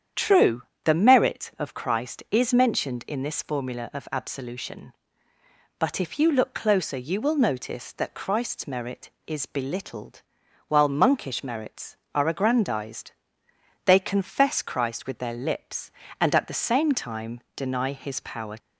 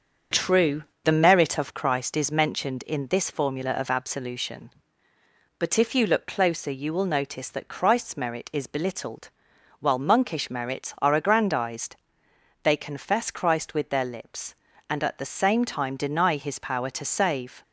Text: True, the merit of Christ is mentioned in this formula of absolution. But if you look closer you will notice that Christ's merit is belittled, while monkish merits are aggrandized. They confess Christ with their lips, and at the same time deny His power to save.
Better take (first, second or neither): second